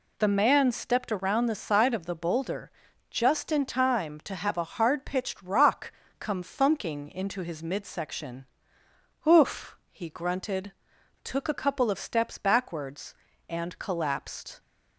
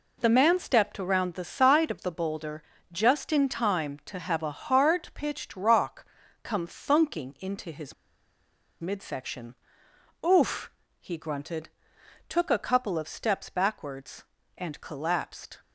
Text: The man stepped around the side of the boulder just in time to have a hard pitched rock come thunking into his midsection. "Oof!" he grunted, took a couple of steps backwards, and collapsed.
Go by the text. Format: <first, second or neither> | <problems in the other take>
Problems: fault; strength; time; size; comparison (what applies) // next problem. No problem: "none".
first | pauses between "boulder" and "just"; slight; at 2.6 s; 0.30 s long; also in the first // pauses between "rock" and "come"; at 6.0 s; 0.38 s long; slight in the first // pauses between "his" and "midsection"; noticeable; at 7.9 s; 0.88 s long